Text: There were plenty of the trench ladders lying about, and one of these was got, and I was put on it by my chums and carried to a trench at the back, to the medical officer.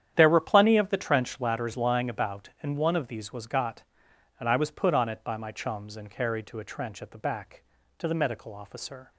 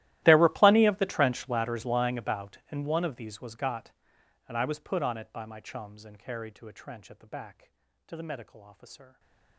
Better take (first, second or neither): first